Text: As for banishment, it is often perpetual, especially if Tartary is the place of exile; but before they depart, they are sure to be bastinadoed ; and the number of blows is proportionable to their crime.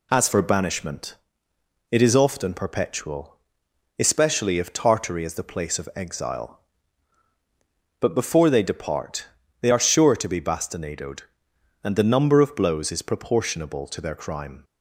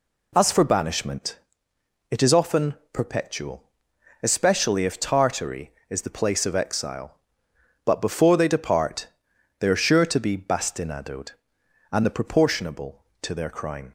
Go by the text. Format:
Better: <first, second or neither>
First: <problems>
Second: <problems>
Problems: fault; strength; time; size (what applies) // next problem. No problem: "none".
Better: first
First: none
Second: pauses between "often" and "perpetual"; slight; at 2.7 s; 0.18 s long // skips "number of blows is"; at 12.0 s